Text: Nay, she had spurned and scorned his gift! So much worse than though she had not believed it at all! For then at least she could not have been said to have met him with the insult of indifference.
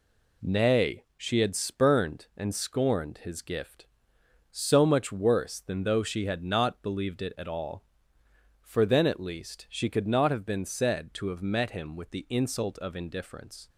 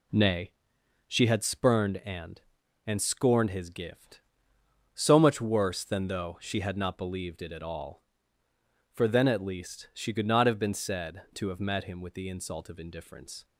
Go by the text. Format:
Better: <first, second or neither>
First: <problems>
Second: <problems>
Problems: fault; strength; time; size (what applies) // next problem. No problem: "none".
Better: first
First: none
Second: says "and" twice; at 2.8 s